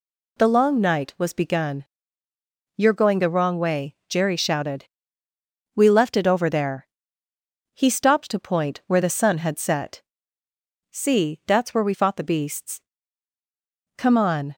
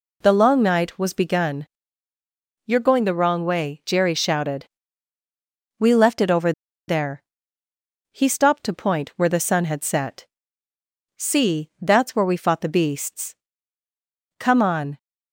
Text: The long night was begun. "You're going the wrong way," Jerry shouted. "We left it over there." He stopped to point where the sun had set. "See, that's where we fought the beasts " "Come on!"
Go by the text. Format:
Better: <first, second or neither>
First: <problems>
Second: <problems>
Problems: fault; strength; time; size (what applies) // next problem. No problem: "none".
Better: first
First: none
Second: pauses between "over" and "there"; at 6.5 s; 0.36 s long